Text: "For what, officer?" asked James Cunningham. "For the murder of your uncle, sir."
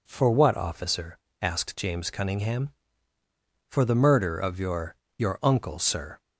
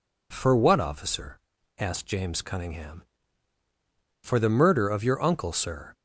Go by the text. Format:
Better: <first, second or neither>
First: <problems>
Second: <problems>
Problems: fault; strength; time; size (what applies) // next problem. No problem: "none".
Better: second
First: says "your" twice; at 5.1 s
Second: none